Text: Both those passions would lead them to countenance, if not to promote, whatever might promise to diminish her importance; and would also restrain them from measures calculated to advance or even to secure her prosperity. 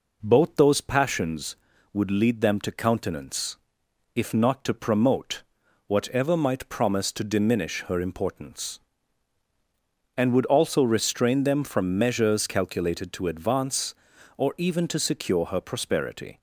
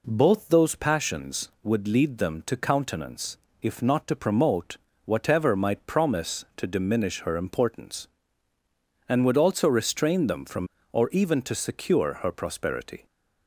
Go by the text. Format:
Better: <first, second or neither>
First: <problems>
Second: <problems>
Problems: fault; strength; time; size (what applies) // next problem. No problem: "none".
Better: first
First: none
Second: skips "measures calculated to advance"; at 10.7 s